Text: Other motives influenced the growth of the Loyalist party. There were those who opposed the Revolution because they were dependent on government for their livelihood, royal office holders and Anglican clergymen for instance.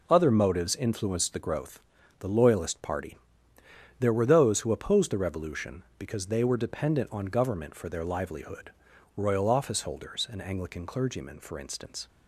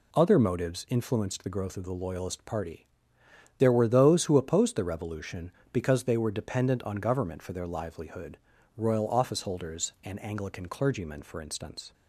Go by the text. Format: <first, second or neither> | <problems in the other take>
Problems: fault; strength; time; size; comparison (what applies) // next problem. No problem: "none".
second | skips "of"; at 1.9 s